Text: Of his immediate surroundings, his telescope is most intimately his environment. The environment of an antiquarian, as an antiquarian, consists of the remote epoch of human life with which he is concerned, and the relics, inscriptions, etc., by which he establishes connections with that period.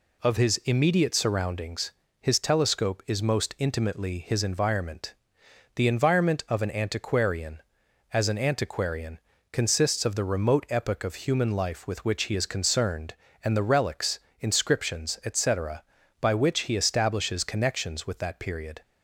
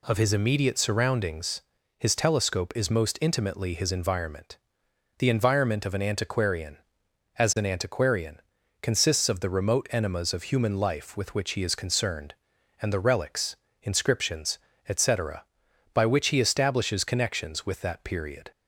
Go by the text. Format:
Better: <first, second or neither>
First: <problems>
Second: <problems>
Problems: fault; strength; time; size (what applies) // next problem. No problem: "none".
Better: first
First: none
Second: says "enemas" for "epoch"; at 9.9 s